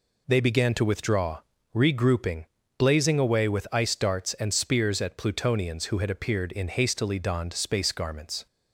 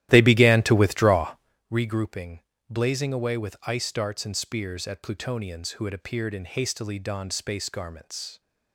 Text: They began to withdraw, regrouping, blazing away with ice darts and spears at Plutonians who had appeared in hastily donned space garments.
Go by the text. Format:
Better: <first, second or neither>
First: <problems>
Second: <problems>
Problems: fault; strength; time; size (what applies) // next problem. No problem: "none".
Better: first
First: none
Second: starts louder than the rest; strong; until 1.6 s; 14 dB